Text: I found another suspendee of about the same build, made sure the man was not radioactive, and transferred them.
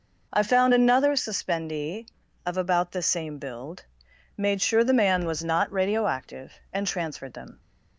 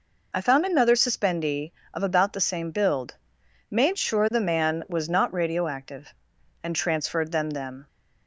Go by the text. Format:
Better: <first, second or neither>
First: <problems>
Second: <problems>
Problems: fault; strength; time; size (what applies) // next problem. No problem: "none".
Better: first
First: none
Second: says "them" twice; at 7.5 s